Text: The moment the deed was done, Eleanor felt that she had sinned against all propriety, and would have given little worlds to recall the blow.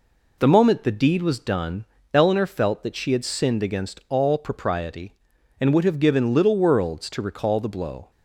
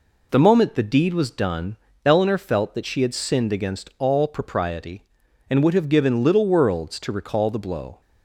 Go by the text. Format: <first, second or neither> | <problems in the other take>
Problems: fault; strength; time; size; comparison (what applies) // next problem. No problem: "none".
neither | none